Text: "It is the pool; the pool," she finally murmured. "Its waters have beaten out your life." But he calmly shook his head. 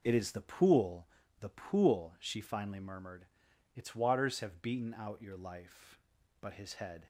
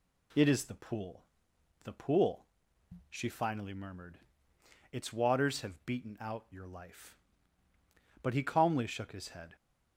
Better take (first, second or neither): second